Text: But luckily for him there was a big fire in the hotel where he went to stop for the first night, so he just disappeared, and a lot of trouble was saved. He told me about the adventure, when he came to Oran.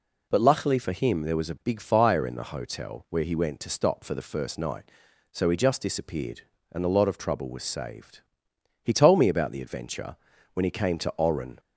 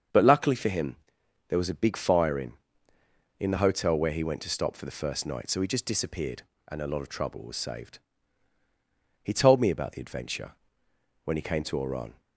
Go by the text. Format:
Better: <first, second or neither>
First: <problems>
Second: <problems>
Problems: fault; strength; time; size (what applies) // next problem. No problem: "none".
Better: first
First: none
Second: starts louder than the rest; until 1.6 s; 6.5 dB // pauses between "him" and "there"; noticeable; at 0.9 s; 0.52 s long // says "in" twice; at 3.3 s